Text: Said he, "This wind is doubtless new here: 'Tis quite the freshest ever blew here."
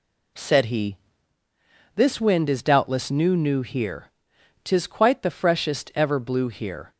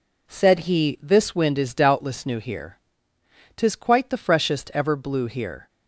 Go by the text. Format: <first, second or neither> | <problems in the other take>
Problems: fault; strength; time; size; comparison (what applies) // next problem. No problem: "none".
second | says "new" twice; at 3.3 s